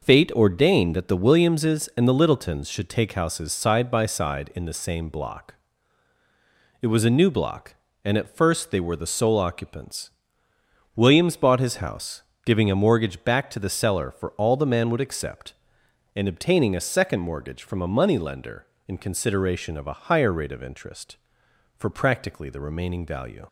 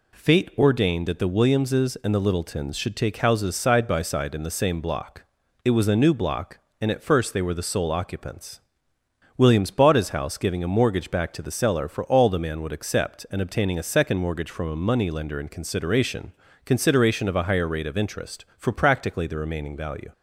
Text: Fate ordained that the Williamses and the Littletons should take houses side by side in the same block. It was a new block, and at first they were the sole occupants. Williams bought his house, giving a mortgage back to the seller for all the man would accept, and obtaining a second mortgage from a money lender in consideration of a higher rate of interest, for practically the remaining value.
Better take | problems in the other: first | says "consideration" twice; at 16.6 s

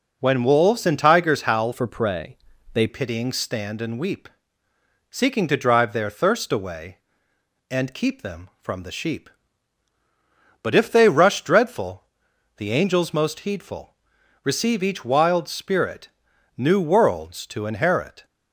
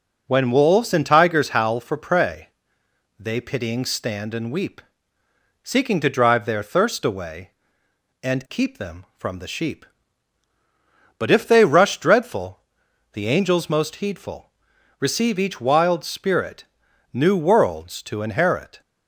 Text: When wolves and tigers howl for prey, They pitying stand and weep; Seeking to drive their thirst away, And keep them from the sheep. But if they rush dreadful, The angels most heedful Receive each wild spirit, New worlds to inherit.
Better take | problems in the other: second | changes voice from "for" to "They"; from 1.7 to 2.8 s; 1.1 s long // pauses between "heedful" and "Receive"; noticeable; at 13.9 s; 0.48 s long; noticeable in the second

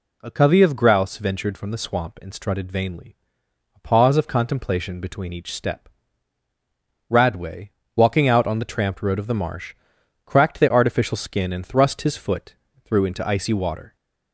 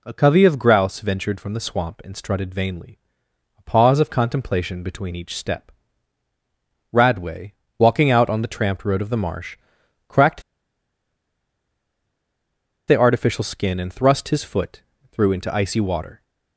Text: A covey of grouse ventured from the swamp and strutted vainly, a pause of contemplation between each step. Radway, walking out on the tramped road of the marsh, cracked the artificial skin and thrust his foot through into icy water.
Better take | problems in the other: first | pauses between "cracked" and "the"; strong; at 10.4 s; 2.4 s long // pauses between "foot" and "through"; slight; at 14.8 s; 0.32 s long; slight in the first

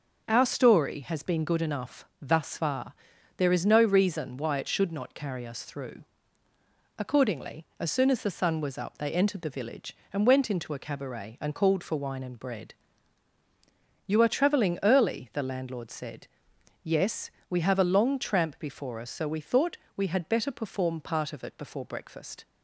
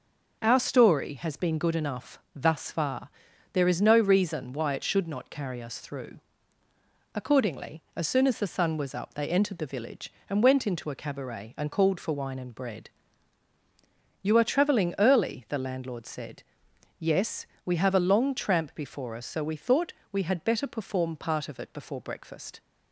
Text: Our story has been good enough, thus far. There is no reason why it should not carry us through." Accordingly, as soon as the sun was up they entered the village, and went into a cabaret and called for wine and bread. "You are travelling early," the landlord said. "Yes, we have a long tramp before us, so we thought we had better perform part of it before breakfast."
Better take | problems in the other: neither | starts louder than the rest; the same in both // pauses between "thought" and "we"; slight; the same in both

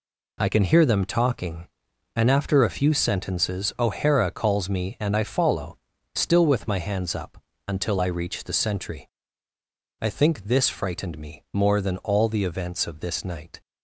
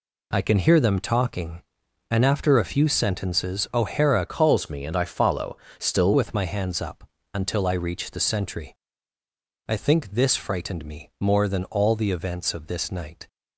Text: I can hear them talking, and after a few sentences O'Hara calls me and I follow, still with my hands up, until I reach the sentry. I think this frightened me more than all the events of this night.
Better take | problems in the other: first | changes voice from "calls" to "still"; from 4.2 to 6.1 s; 1.9 s long

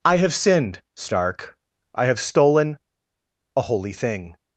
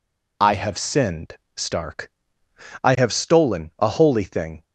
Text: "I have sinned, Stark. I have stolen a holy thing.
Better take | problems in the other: second | pauses between "stolen" and "a"; noticeable; at 2.7 s; 0.76 s long

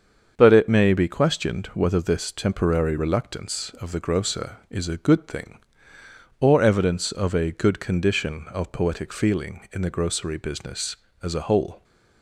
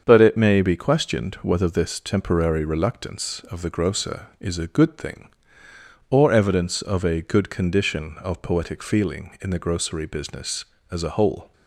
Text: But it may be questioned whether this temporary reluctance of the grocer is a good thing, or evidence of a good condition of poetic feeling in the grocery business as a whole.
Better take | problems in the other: neither | starts louder than the rest; the same in both

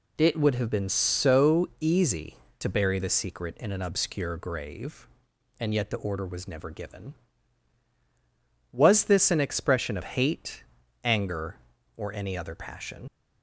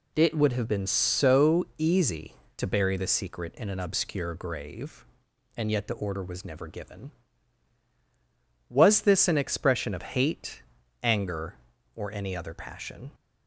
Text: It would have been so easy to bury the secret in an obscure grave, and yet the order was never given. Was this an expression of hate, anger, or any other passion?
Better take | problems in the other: second | leaves "passion" unfinished; at 13.0 s; 75 ms

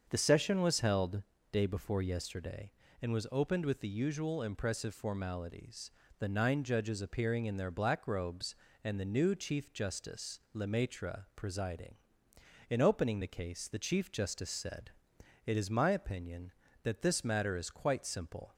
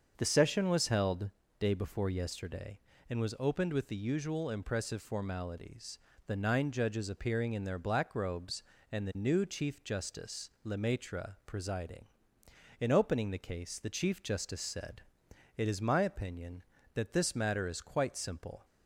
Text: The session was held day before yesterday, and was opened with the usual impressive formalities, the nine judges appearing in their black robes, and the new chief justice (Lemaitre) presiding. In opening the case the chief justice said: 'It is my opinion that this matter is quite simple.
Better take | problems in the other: neither | starts louder than the rest; the same in both // pauses between "held" and "day"; slight; the same in both

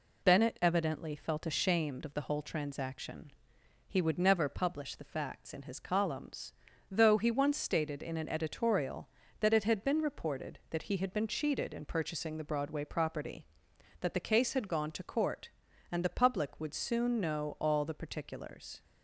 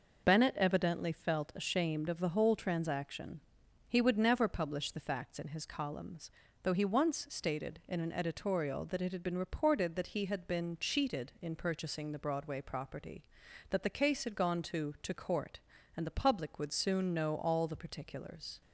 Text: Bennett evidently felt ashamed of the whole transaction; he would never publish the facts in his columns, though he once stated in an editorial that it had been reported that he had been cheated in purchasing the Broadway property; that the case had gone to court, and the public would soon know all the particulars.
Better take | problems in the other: first | says "to" twice; at 15.0 s

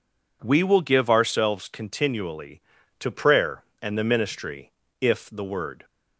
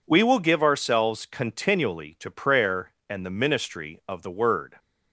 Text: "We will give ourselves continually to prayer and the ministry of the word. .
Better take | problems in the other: second | says "if" for "of"; at 4.9 s

